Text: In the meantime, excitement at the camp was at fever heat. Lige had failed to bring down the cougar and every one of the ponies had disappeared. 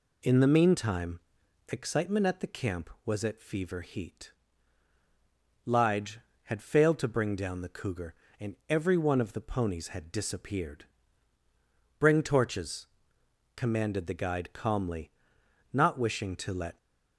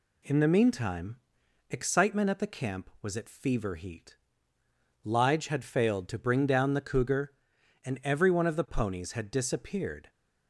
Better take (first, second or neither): second